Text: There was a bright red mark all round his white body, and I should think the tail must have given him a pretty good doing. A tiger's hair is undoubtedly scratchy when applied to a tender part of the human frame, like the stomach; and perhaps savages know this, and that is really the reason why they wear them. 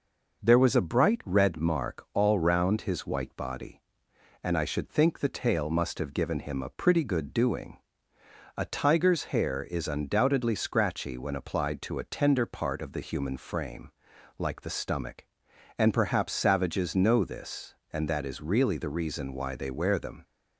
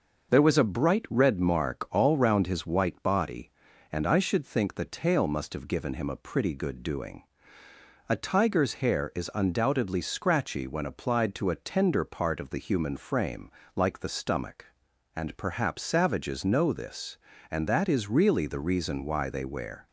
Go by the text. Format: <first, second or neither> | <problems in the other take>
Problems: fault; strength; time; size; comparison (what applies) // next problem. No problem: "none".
first | stops before "them"; at 19.8 s